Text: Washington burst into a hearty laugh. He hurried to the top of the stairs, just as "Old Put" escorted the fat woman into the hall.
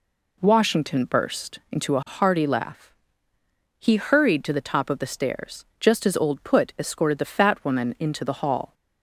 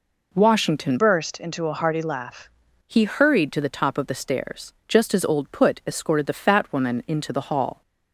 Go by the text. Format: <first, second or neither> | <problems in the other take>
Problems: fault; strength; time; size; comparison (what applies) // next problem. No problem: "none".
first | changes voice from "burst" to "laugh"; from 0.9 to 2.4 s; 1.5 s long